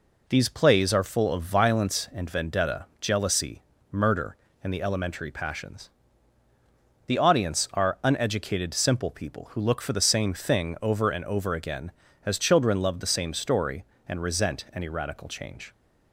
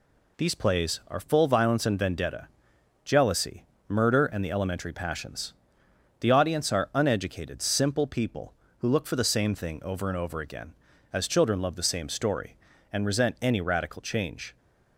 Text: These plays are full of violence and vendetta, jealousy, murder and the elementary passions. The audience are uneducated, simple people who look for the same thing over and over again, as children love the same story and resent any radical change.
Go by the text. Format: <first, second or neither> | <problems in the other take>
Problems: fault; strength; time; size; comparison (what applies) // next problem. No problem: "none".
first | skips "of"; at 1.4 s